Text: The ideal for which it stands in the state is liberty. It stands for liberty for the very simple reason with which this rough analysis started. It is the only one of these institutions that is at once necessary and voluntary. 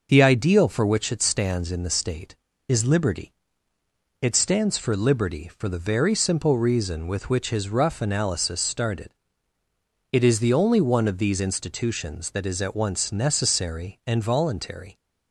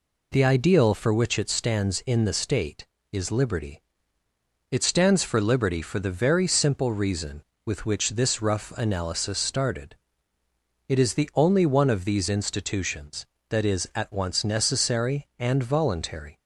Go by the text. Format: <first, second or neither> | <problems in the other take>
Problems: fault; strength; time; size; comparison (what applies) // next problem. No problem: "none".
second | says "his" for "this"; at 7.5 s